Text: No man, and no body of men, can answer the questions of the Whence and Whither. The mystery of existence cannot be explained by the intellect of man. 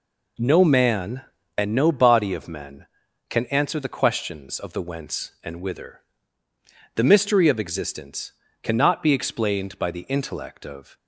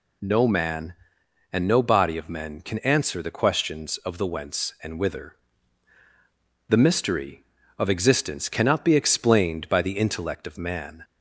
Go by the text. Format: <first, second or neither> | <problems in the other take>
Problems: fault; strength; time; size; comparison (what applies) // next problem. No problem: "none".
second | pauses between "existence" and "cannot"; slight; at 8.3 s; 0.28 s long // stops before "man"; at 10.9 s